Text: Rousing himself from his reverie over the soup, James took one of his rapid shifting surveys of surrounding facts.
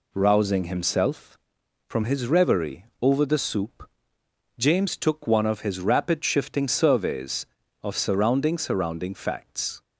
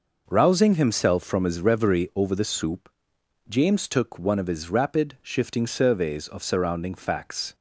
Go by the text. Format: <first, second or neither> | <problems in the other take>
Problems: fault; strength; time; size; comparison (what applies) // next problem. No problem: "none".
second | says "surrounding" twice; at 8.5 s